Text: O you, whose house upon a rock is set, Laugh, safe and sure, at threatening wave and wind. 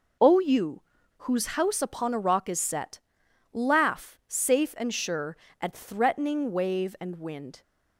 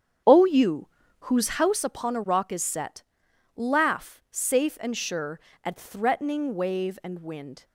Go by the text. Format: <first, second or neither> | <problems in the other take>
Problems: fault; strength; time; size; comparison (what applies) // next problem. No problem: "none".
first | starts louder than the rest; strong; until 1.8 s; 8.5 dB